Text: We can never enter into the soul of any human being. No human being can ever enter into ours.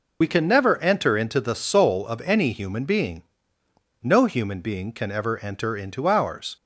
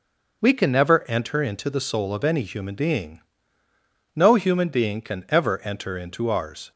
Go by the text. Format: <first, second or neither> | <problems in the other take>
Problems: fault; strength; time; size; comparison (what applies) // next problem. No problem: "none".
second | loses the start of "We"; at 0.2 s; 45 ms